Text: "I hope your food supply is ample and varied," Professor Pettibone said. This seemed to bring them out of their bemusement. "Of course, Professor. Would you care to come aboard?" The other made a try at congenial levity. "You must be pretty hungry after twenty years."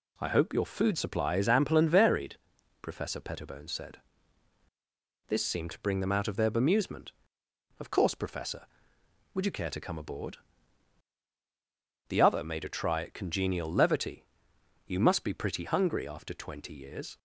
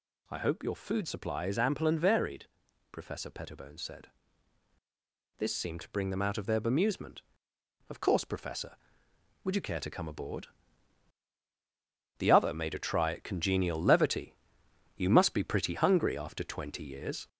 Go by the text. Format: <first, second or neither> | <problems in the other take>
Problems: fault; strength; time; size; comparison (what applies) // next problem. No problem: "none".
first | gets louder; slight; throughout; 3 dB